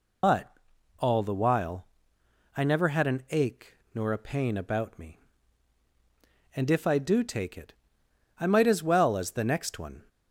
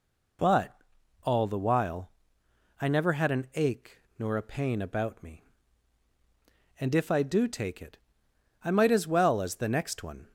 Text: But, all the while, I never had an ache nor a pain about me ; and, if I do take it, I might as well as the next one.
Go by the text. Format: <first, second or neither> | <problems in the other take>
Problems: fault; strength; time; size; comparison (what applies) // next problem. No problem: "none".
second | loses the start of "But"; at 0.2 s; 85 ms // pauses between "ache" and "nor"; slight; at 3.7 s; 0.20 s long; slight in the second